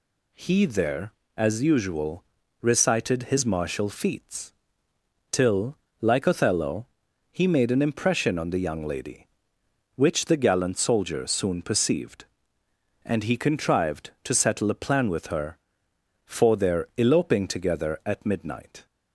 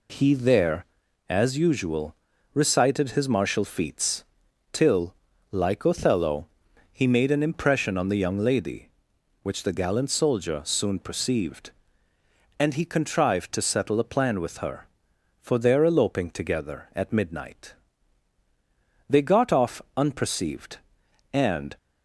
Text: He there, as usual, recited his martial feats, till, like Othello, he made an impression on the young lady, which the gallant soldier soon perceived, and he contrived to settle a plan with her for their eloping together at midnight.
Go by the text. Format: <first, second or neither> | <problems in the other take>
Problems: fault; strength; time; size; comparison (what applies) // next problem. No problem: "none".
first | goes on to say "They got off unperceived and"; strong; from 19.0 s on; 2.6 s long